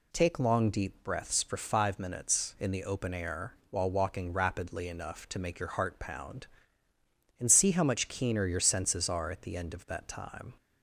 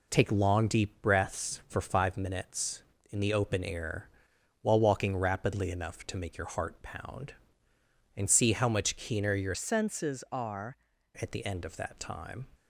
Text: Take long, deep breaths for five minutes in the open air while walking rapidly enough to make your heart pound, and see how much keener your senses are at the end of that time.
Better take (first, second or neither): first